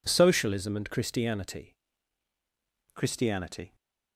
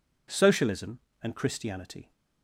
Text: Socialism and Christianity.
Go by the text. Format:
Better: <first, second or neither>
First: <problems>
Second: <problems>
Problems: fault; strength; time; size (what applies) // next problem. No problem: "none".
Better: second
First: says "Christianity" twice; at 2.9 s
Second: none